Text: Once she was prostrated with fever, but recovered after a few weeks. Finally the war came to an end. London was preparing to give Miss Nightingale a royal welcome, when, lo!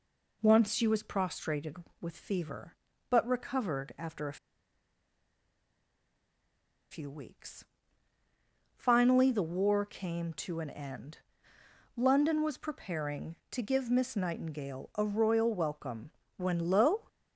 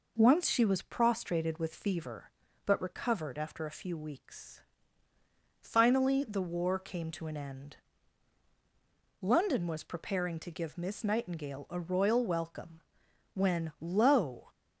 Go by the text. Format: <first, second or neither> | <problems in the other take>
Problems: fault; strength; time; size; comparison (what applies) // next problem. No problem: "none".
second | pauses between "a" and "few"; strong; at 4.3 s; 2.5 s long